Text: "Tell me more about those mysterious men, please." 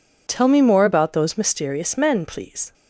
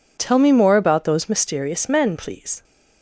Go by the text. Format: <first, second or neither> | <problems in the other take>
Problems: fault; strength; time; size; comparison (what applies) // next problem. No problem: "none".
neither | none